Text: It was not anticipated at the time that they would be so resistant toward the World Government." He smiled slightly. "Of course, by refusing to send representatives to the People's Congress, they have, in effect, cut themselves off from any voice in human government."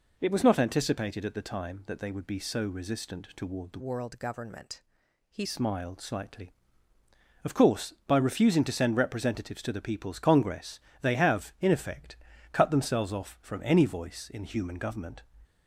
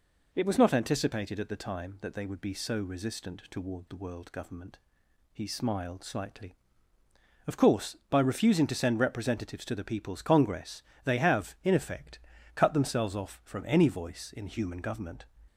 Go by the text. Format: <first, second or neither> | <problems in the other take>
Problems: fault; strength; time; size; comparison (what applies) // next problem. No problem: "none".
second | changes voice from "World" to "He"; from 3.7 to 5.4 s; 1.7 s long